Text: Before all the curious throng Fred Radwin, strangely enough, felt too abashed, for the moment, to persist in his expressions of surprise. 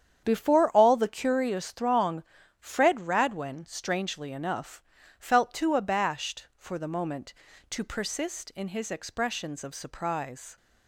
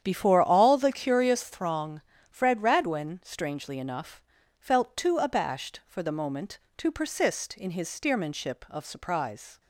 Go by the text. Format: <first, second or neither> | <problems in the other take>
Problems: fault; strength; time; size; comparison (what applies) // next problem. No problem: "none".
first | starts louder than the rest; strong; until 1.0 s; 9.5 dB; strong in the first // pauses between "throng" and "Fred"; slight; at 2.0 s; 0.30 s long; slight in the first // says "steermanship" for "expressions"; at 7.9 s